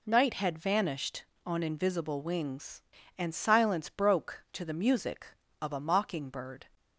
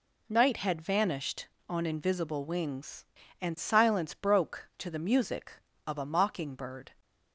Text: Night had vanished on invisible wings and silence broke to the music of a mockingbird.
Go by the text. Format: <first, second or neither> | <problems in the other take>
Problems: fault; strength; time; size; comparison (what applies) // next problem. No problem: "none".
neither | none